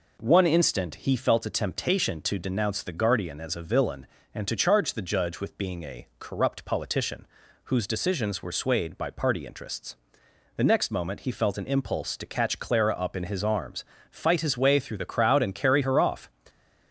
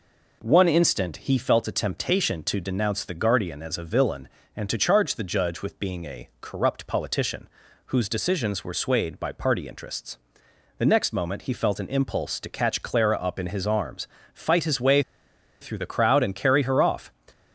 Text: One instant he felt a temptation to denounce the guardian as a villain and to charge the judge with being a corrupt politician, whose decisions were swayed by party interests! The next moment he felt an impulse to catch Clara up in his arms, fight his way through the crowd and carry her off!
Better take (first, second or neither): first